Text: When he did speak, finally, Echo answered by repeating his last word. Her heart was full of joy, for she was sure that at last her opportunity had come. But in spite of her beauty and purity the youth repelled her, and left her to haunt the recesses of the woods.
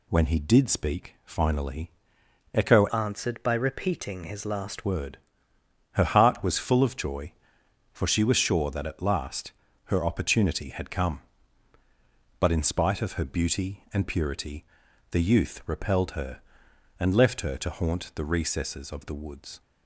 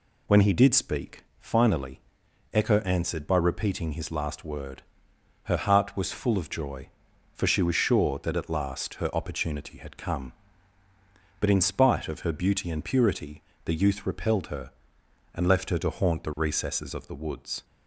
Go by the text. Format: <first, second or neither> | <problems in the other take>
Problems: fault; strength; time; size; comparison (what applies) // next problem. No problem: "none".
second | changes voice from "answered" to "last"; from 2.8 to 4.8 s; 2.0 s long // pauses between "last" and "her"; slight; at 9.5 s; 0.34 s long // pauses between "purity" and "the"; noticeable; at 14.6 s; 0.48 s long; slight in the second